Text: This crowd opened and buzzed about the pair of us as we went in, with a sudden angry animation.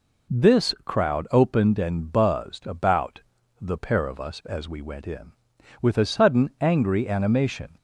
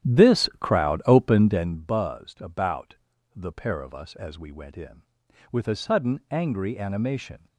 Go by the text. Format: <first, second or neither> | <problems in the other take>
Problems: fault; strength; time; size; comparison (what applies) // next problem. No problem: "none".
first | starts louder than the rest; strong; until 1.8 s; 11.5 dB // pauses between "about" and "the"; slight; at 2.9 s; 0.36 s long; slight in the first